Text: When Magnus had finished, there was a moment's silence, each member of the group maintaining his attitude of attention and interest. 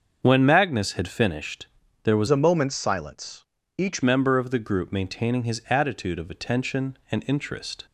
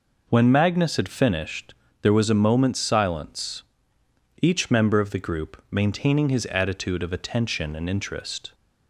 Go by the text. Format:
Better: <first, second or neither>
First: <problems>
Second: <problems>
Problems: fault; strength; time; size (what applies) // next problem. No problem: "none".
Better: second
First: starts louder than the rest; until 1.2 s; 6.5 dB // changes voice from "a" to "each"; from 2.2 to 4.0 s; 1.8 s long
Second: none